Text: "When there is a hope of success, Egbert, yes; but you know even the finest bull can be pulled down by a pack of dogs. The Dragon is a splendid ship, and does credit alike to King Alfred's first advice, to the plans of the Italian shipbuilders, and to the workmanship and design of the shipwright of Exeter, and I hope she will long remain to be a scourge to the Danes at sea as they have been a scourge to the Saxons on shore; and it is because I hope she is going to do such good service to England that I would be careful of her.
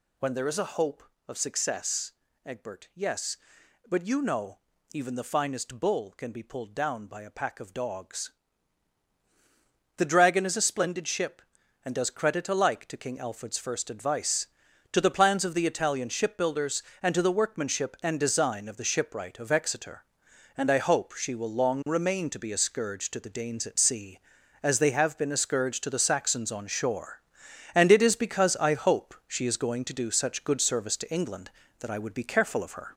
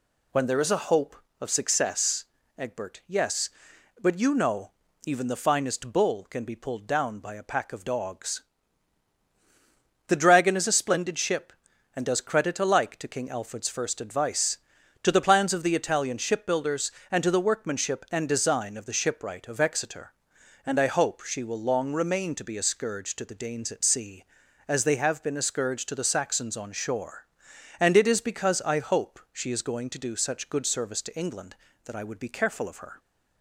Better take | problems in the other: second | gets louder; noticeable; throughout; 5 dB // pauses between "know" and "even"; slight; at 4.5 s; 0.34 s long; slight in the second

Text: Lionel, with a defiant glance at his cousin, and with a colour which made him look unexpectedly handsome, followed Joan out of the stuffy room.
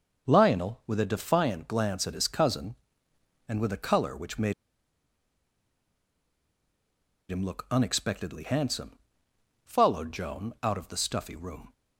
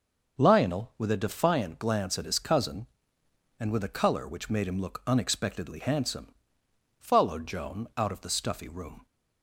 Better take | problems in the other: second | pauses between "made" and "him"; strong; at 4.5 s; 2.7 s long

